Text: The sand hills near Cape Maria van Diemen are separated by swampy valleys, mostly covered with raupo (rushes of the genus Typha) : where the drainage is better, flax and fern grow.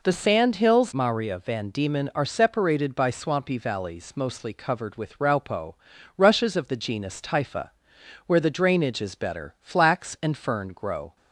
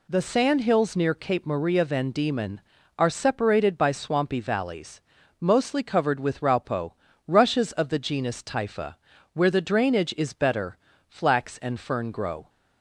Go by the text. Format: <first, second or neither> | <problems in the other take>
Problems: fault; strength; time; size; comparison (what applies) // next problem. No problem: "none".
second | skips "near Cape"; at 0.9 s